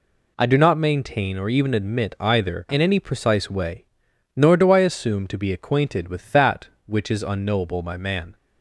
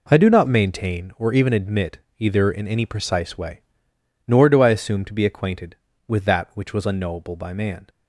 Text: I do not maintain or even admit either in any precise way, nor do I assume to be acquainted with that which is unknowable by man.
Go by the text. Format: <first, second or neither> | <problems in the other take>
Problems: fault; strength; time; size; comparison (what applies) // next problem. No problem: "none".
first | pauses between "admit" and "either"; slight; at 1.9 s; 0.20 s long // says "was" for "is"; at 6.7 s